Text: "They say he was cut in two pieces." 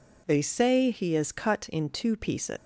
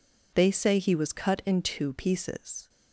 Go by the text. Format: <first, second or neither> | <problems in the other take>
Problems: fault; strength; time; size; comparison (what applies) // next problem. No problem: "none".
second | says "is" for "was"; at 1.1 s